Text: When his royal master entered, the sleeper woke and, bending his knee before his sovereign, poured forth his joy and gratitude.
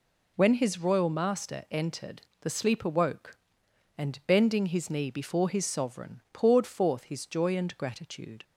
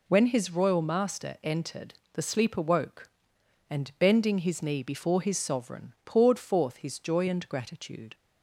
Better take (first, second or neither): neither